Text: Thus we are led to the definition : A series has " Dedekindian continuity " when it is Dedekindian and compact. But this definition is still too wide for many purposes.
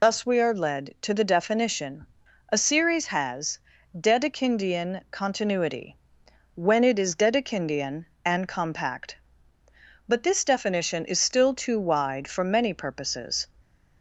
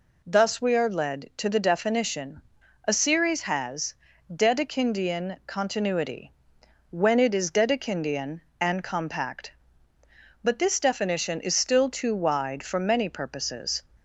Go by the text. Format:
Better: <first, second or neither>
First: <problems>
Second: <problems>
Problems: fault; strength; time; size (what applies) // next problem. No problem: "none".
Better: second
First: loses the start of "Thus"; at 0.0 s; 135 ms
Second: none